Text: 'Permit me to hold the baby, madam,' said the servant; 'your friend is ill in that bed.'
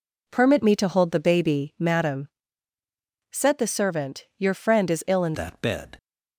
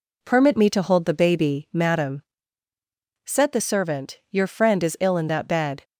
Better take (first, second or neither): second